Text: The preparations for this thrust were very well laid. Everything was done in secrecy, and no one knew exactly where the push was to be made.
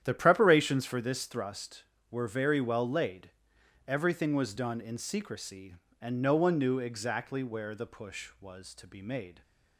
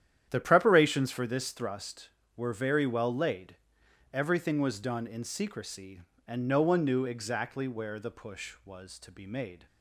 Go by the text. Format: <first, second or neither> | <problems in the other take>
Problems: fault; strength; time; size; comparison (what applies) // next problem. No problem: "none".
neither | starts louder than the rest; strong; the same in both